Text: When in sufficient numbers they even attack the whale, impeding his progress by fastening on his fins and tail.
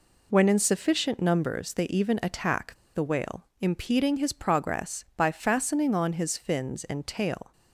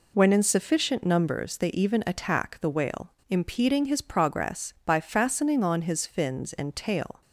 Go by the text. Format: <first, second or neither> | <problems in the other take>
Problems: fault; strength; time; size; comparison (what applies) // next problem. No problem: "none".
second | pauses between "attack" and "the"; slight; at 2.7 s; 0.19 s long